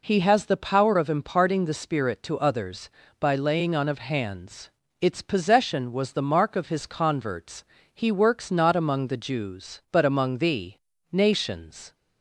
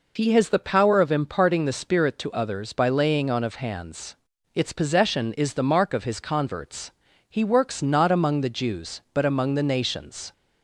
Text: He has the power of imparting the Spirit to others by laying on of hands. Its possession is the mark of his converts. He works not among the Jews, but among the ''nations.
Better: second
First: says "was" for "is"; at 5.9 s // pauses between "the" and "nations"; slight; at 10.7 s; 0.36 s long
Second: none

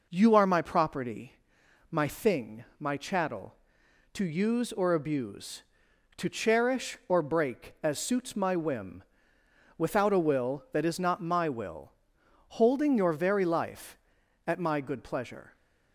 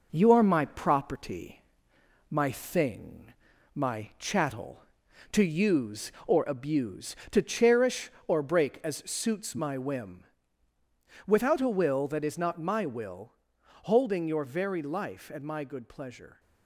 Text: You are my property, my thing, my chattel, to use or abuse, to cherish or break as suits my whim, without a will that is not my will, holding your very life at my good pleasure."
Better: first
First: none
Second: gets quieter; slight; throughout; 3 dB

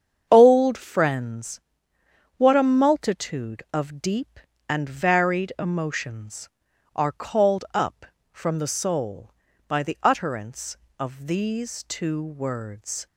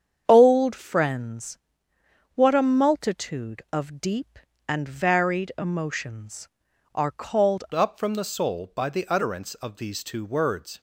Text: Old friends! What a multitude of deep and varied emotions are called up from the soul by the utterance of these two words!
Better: first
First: starts louder than the rest; strong; until 1.3 s; 7.5 dB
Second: starts louder than the rest; strong; until 1.2 s; 8 dB // changes voice at "up"; from 7.7 s on; 3.0 s long

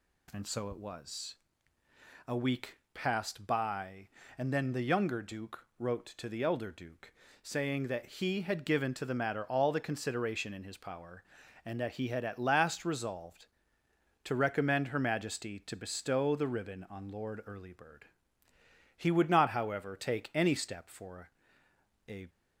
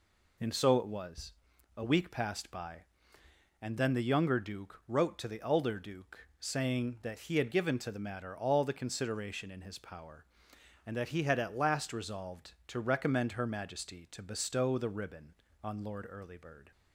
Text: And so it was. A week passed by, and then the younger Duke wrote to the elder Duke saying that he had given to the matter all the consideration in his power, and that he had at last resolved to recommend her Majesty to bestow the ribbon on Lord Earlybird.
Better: second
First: pauses between "week" and "passed"; slight; at 2.7 s; 0.16 s long // pauses between "Duke" and "saying"; slight; at 7.1 s; 0.28 s long // goes on to say "He would not however take any step for a"; strong; from 18.9 s on; 3.3 s long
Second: none

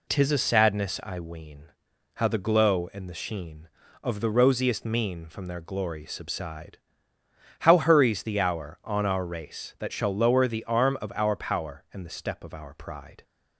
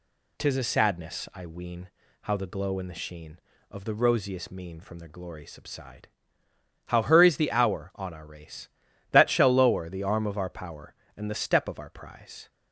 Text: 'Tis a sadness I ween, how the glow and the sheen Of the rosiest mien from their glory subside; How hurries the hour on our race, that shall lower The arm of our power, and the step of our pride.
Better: first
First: none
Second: says "prize" for "pride"; at 11.8 s

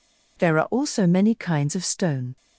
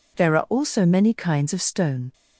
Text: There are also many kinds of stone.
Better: neither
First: none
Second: none

